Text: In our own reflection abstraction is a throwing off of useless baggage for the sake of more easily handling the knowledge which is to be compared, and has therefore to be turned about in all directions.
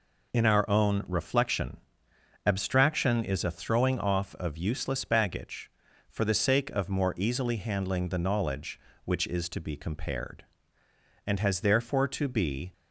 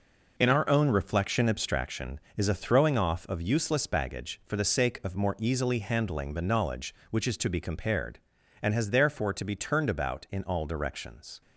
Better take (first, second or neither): second